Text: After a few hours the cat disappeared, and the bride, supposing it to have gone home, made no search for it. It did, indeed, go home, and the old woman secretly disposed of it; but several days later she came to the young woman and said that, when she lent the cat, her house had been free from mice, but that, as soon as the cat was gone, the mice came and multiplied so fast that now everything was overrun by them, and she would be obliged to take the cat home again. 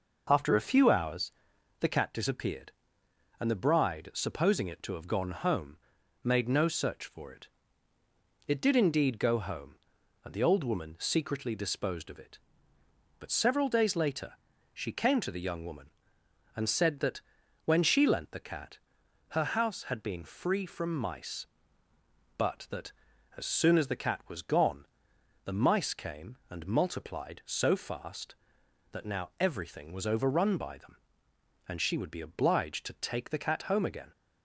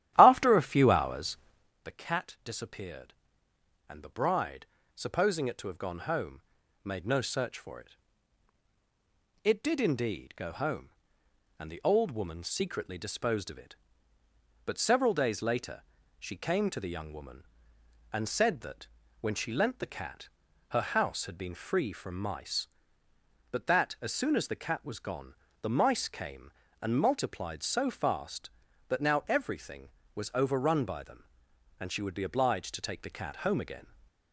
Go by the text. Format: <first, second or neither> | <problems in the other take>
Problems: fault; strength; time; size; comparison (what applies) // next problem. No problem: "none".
first | starts louder than the rest; strong; until 1.7 s; 13 dB // pauses between "hours" and "the"; noticeable; at 1.3 s; 0.46 s long; noticeable in the first // pauses between "later" and "she"; at 15.8 s; 0.38 s long; also in the first